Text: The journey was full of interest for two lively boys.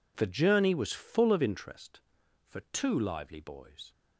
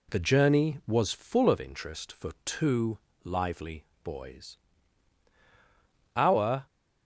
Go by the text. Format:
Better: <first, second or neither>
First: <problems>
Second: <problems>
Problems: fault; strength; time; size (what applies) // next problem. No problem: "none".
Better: first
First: none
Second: pauses between "two" and "lively"; slight; at 2.9 s; 0.26 s long // pauses between "lively" and "boys"; slight; at 3.8 s; 0.18 s long // goes on to say "Our"; from 6.1 s on; 0.50 s long